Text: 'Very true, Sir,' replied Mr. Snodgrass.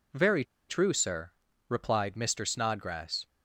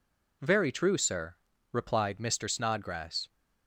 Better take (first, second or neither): second